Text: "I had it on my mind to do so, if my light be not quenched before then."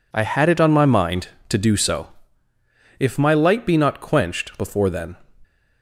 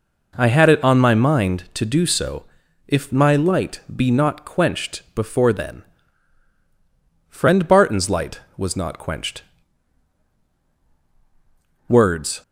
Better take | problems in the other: first | goes on to say "Friend Barton's light was not quenched Words"; strong; from 7.2 s on; 5.1 s long

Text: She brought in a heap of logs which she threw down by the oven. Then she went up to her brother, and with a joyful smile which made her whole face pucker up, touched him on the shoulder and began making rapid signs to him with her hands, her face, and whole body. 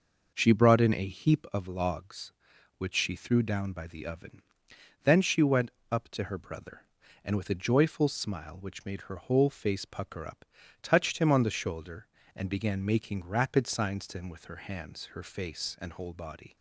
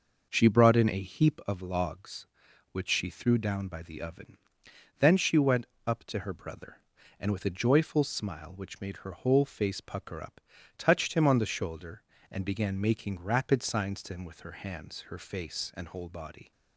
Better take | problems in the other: neither | pauses between "went" and "up"; slight; the same in both

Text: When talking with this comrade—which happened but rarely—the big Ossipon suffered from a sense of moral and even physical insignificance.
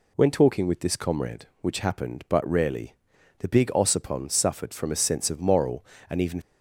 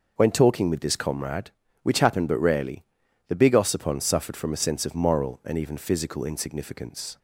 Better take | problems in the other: second | stops before "physical insignificance"; at 6.4 s

